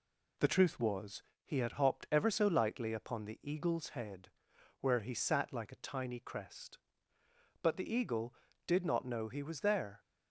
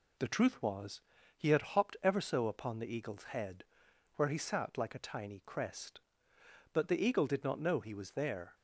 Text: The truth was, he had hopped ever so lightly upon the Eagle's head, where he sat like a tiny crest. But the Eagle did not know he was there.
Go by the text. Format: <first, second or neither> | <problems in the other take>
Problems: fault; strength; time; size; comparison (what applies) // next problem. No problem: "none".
first | skips "lightly"; at 2.4 s